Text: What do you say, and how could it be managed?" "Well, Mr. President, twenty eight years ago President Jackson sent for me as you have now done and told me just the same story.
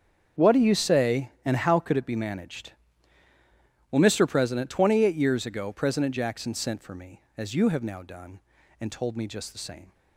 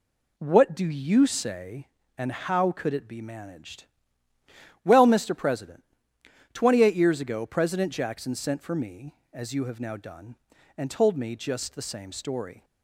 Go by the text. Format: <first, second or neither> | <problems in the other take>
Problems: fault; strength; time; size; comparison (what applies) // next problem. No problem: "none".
second | starts louder than the rest; strong; until 1.5 s; 7.5 dB // stops before "story"; at 9.9 s